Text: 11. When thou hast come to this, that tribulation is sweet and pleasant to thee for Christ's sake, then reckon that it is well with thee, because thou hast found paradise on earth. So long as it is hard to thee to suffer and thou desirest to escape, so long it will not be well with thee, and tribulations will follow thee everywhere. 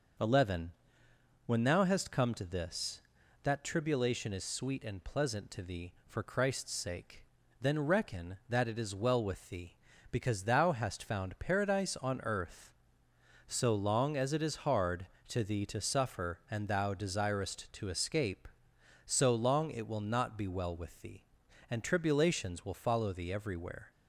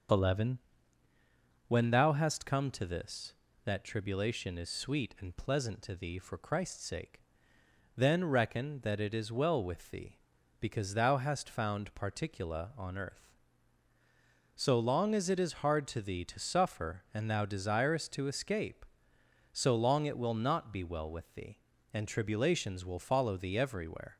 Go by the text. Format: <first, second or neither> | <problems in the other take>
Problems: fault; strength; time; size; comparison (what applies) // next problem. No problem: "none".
first | starts louder than the rest; until 2.2 s; 6.5 dB // says "particula" for "paradise"; at 11.9 s